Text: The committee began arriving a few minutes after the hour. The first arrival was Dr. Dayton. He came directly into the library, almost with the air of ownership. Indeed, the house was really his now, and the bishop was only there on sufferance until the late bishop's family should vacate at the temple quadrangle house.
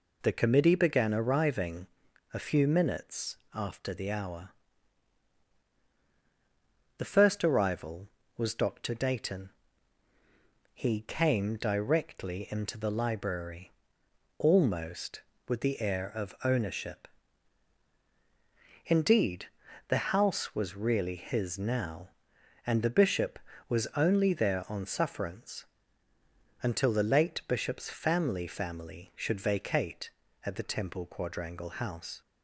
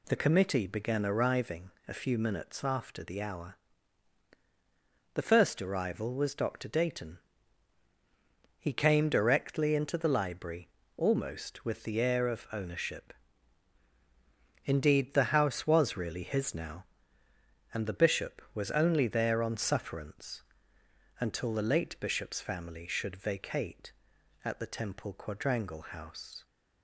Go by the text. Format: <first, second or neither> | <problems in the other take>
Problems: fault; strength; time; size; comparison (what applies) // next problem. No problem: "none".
second | pauses between "arriving" and "a"; noticeable; at 1.8 s; 0.46 s long; slight in the second // pauses between "minutes" and "after"; slight; at 3.3 s; 0.18 s long // pauses between "sufferance" and "until"; noticeable; at 25.6 s; 0.96 s long; noticeable in the second // says "family" twice; at 28.4 s